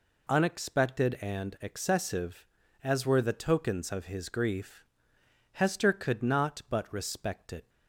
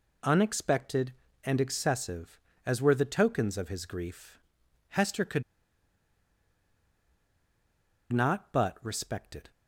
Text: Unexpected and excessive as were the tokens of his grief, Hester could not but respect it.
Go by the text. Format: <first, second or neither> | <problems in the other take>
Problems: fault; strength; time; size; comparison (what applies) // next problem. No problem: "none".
first | pauses between "could" and "not"; strong; at 5.4 s; 2.6 s long